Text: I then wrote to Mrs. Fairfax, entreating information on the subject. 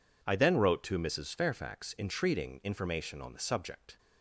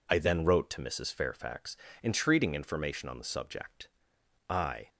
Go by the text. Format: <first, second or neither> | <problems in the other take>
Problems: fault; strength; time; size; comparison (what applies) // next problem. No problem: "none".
first | goes on to say "I"; slight; from 4.5 s on; 0.38 s long